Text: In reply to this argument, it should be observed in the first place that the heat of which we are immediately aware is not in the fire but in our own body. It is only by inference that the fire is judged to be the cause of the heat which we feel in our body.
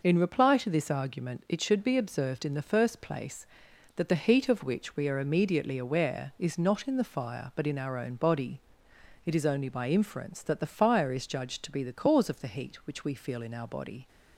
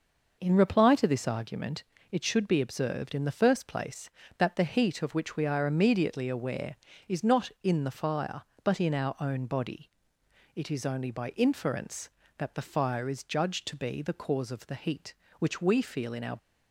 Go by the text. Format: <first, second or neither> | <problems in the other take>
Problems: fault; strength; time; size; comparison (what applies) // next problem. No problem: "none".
first | stops before "body"; at 16.3 s